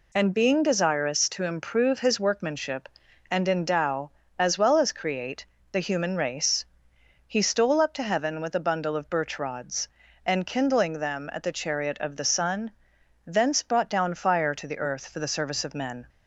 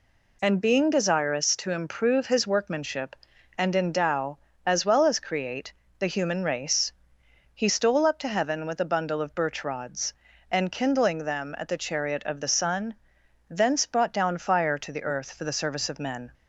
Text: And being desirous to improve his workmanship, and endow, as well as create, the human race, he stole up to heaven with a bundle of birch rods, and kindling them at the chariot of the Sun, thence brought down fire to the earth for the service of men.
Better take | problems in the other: neither | none

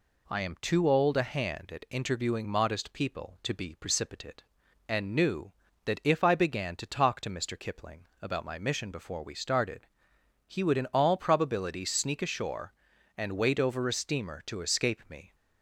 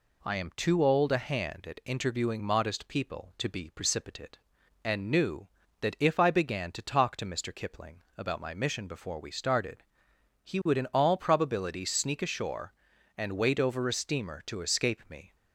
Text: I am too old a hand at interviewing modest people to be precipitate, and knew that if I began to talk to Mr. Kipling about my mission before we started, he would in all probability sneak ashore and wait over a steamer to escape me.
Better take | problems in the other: neither | none

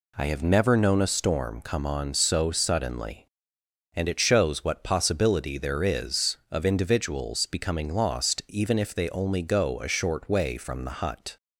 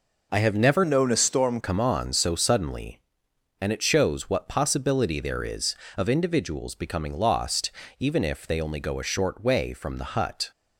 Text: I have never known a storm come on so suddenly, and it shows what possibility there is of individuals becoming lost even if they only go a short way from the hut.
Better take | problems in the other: first | changes voice from "known" to "storm"; from 0.8 to 1.5 s; 0.7 s long // pauses between "lost" and "even"; slight; at 7.7 s; 0.28 s long

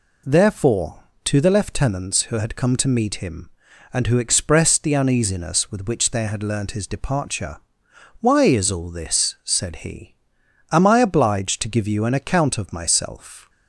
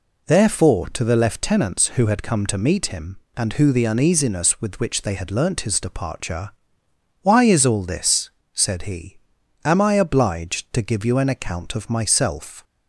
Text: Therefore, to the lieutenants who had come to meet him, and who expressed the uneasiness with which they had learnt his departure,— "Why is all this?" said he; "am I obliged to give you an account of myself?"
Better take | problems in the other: first | skips "expressed"; at 3.7 s

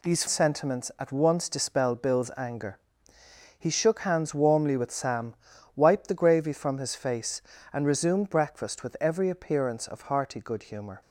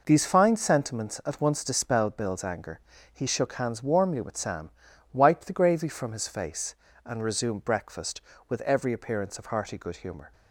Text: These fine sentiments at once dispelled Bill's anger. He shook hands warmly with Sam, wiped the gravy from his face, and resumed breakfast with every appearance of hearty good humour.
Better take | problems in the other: second | skips "fine"; at 0.2 s

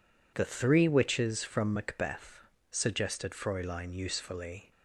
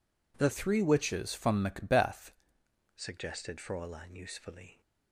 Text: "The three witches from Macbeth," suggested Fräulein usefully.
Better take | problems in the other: first | changes voice from "three" to "Macbeth"; from 0.5 to 2.3 s; 1.8 s long

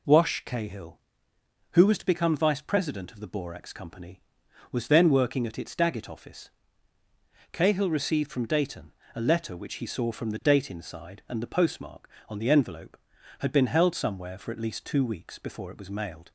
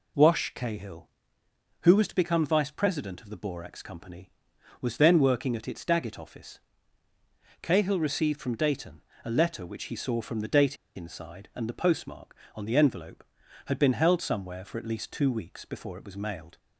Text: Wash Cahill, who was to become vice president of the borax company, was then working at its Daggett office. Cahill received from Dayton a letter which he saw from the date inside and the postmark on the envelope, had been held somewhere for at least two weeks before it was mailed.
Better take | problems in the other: first | pauses between "Dayton" and "a"; slight; at 9.0 s; 0.24 s long; slight in the first // pauses between "date" and "inside"; slight; at 10.7 s; 0.21 s long

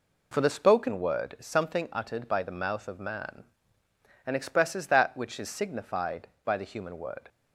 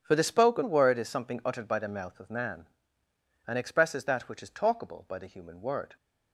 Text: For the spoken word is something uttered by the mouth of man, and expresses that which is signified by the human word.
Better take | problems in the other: first | starts louder than the rest; strong; until 1.0 s; 8.5 dB // says "talkable" for "signified"; at 4.4 s

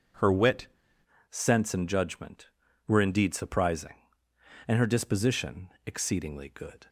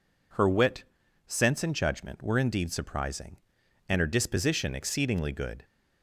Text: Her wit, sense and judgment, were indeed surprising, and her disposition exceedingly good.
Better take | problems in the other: second | changes voice at "sense"; from 1.3 s on; 5.5 s long // pauses between "disposition" and "exceedingly"; slight; at 5.7 s; 0.16 s long

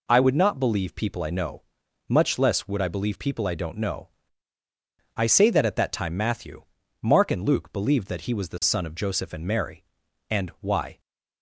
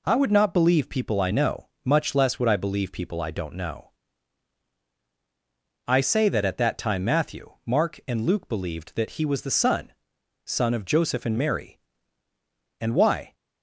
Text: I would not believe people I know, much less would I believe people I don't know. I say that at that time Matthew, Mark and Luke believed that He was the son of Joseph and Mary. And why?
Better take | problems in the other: first | says "son" twice; at 10.4 s

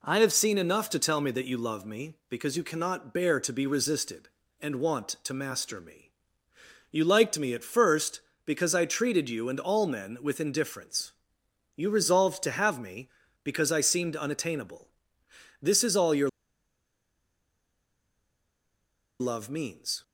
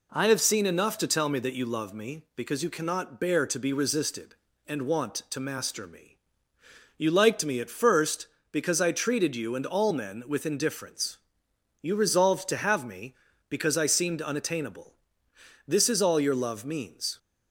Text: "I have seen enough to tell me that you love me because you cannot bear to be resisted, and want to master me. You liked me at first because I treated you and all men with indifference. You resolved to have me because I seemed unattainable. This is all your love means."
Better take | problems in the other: second | pauses between "your" and "love"; strong; at 16.2 s; 2.9 s long

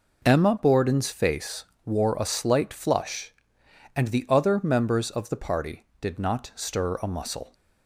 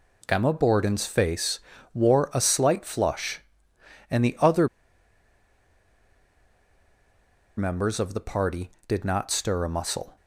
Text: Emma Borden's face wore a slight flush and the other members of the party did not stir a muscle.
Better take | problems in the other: first | pauses between "face" and "wore"; slight; at 1.5 s; 0.34 s long; slight in the first // pauses between "other" and "members"; strong; at 4.6 s; 2.9 s long

